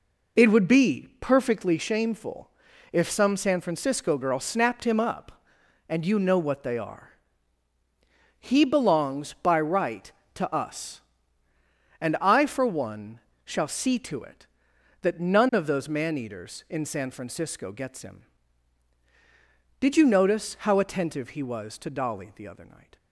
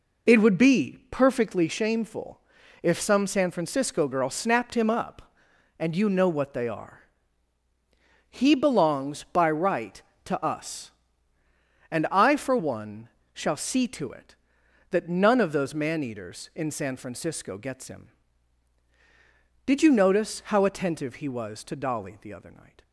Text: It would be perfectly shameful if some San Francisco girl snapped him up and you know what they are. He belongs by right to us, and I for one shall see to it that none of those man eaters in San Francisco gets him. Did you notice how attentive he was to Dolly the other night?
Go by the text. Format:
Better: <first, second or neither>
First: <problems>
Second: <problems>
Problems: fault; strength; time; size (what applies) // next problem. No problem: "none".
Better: neither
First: pauses between "shameful" and "if"; at 2.5 s; 0.42 s long // pauses between "one" and "shall"; slight; at 13.1 s; 0.26 s long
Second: pauses between "shameful" and "if"; at 2.4 s; 0.42 s long // pauses between "one" and "shall"; slight; at 13.0 s; 0.26 s long